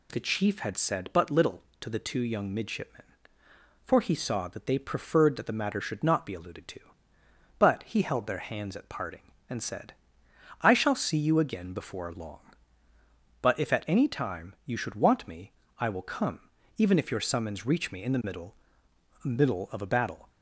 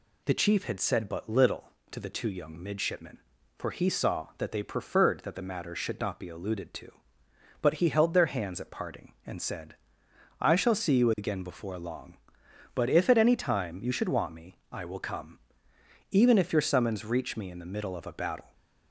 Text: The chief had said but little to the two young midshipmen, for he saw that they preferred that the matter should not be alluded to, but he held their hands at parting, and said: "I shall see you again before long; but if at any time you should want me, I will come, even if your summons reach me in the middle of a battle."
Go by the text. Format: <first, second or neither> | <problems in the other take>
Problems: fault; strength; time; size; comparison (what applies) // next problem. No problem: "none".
second | says "middle" twice; at 19.2 s